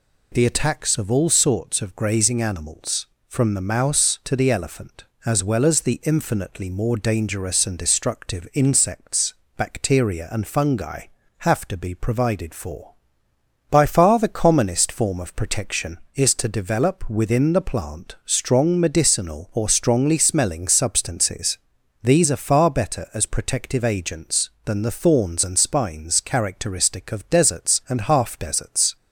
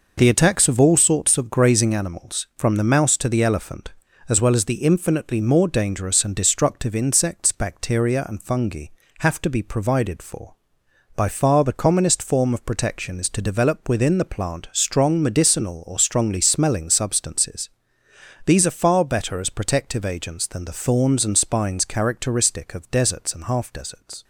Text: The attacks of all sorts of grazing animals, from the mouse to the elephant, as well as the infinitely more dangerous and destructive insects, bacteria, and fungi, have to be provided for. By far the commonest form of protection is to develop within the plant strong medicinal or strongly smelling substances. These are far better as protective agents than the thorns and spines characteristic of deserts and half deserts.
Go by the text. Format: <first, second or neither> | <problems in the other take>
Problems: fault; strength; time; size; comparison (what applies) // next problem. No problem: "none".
neither | none